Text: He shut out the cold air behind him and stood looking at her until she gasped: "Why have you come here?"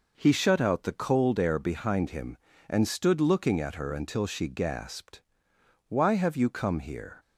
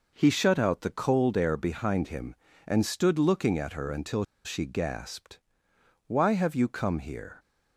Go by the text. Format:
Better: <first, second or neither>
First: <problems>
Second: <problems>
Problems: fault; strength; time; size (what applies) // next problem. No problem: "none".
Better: first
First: none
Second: pauses between "until" and "she"; slight; at 4.2 s; 0.21 s long